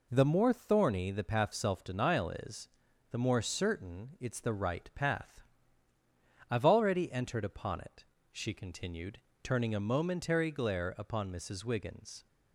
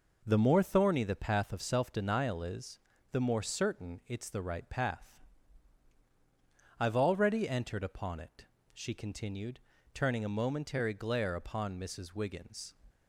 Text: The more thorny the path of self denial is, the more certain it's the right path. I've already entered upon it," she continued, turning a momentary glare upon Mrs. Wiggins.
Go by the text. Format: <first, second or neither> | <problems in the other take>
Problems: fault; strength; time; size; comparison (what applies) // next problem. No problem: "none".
second | skips "of"; at 1.5 s